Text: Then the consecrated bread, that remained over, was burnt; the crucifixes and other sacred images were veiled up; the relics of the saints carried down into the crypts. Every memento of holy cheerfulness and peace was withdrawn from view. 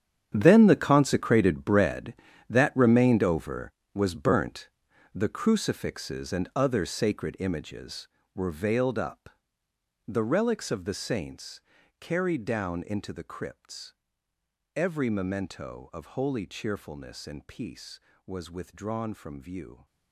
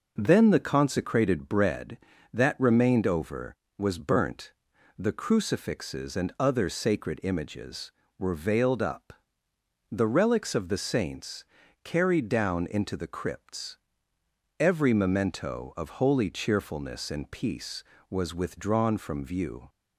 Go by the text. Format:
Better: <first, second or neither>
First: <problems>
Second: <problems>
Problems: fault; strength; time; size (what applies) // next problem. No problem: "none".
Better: second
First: gets quieter; strong; throughout; 14.5 dB // pauses between "saints" and "carried"; at 11.6 s; 0.38 s long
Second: pauses between "saints" and "carried"; at 11.4 s; 0.38 s long